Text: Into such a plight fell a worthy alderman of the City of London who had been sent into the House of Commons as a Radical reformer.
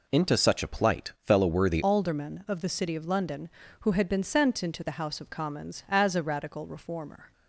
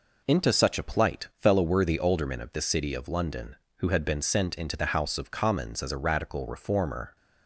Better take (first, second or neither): second